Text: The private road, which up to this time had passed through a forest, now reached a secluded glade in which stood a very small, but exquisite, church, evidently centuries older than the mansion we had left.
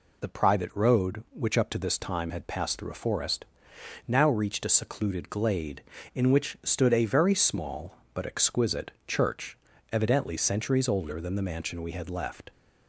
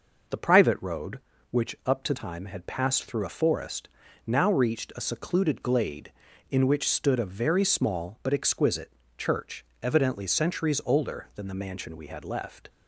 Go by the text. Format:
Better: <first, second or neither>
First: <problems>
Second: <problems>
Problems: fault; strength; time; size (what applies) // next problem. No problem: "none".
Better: first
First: none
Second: skips "this"; at 2.1 s